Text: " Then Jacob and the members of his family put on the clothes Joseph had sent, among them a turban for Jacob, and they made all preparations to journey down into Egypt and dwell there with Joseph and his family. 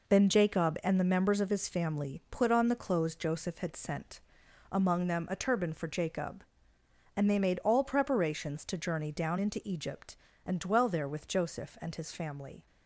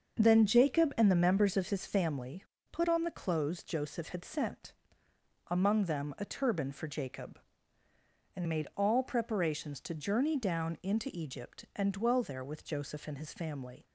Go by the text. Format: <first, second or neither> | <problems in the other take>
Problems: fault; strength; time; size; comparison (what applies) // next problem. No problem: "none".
first | starts louder than the rest; until 1.2 s; 6.5 dB // pauses between "family" and "put"; slight; at 2.4 s; 0.30 s long // skips "they"; at 8.4 s